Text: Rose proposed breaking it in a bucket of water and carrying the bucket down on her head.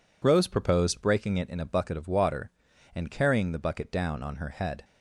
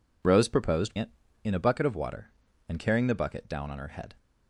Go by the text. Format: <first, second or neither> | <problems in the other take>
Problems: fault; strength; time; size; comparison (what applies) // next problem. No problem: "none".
first | skips "breaking"; at 0.9 s